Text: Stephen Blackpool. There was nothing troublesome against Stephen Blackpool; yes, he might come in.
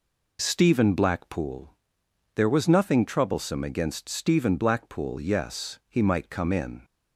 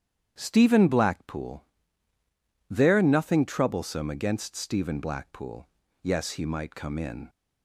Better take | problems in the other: first | starts louder than the rest; strong; until 1.3 s; 9.5 dB // skips "was"; at 3.0 s

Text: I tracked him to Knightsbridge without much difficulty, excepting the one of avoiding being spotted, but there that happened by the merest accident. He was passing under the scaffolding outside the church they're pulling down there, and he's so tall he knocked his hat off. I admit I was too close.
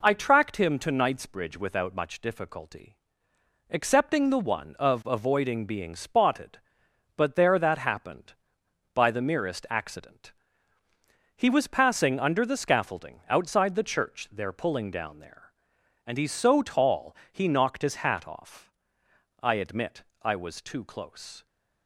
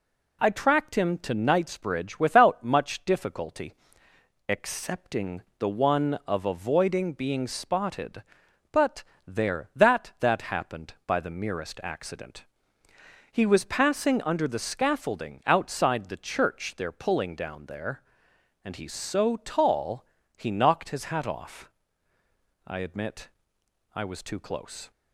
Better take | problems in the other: first | pauses between "excepting" and "the"; slight; at 5.4 s; 0.18 s long // pauses between "but" and "there"; slight; at 9.0 s; 0.24 s long // says "that" twice; at 10.1 s // pauses between "tall" and "he"; slight; at 20.0 s; 0.32 s long; slight in the first // pauses between "admit" and "I"; noticeable; at 23.3 s; 0.64 s long; slight in the first

